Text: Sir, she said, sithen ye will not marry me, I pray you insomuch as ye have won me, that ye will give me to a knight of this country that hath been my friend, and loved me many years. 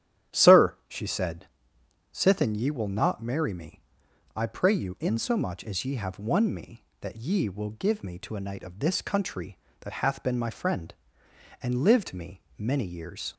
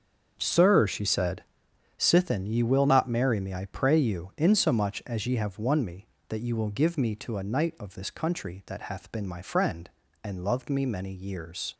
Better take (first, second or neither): second